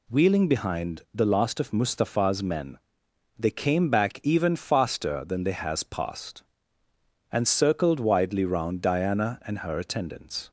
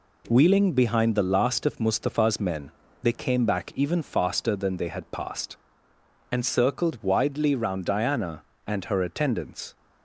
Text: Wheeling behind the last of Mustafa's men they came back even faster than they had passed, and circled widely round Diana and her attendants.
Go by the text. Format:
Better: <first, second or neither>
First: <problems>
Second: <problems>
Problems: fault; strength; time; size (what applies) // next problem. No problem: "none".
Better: second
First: pauses between "men" and "they"; noticeable; at 2.7 s; 0.58 s long // says "has" for "had"; at 5.5 s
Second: pauses between "men" and "they"; slight; at 2.7 s; 0.32 s long